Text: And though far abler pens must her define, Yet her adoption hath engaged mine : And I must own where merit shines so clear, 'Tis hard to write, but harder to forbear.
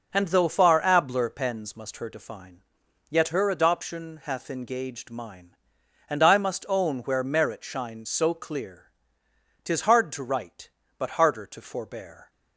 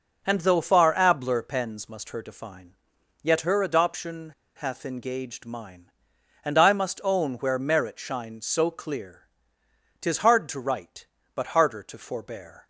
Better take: first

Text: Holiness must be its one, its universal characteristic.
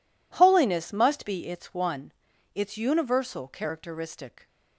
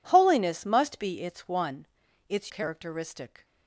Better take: first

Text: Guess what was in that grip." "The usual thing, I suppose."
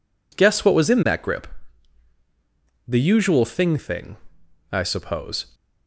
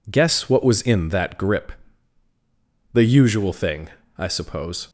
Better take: second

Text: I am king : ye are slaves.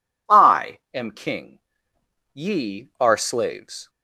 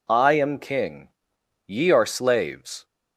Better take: neither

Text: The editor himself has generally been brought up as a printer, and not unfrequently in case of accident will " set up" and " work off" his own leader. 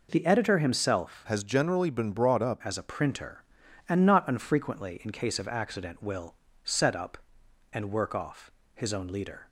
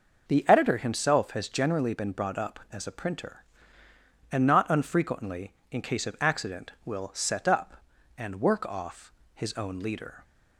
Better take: second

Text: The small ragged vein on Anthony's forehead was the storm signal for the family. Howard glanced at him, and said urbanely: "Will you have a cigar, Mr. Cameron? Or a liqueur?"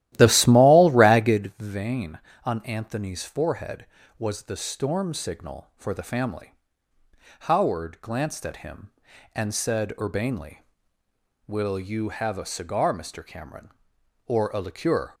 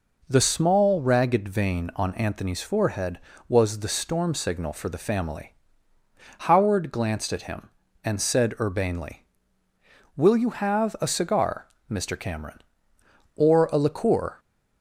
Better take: second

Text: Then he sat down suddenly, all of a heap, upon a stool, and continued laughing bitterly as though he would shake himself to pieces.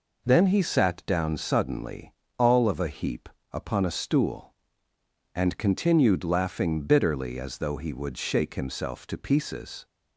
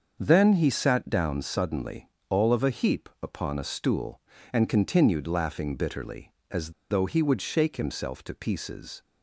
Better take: first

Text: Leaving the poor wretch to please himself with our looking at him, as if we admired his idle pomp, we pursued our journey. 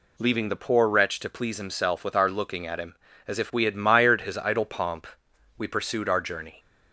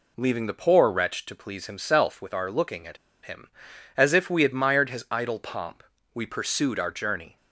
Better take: first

